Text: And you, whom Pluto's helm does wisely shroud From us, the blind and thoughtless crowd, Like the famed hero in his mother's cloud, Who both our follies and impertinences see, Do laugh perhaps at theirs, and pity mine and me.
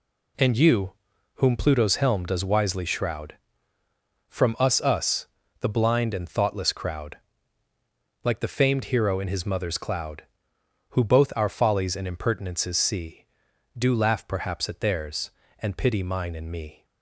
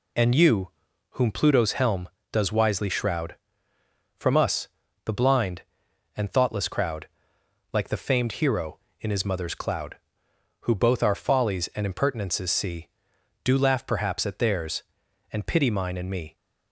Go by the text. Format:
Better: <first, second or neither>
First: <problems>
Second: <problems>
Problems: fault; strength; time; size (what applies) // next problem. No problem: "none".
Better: second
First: says "us" twice; at 4.8 s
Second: none